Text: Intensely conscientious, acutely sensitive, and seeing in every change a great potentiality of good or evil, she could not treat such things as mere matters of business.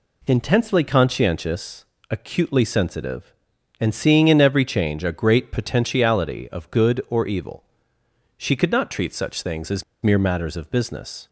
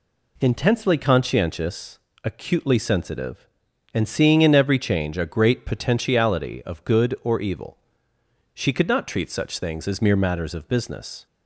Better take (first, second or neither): second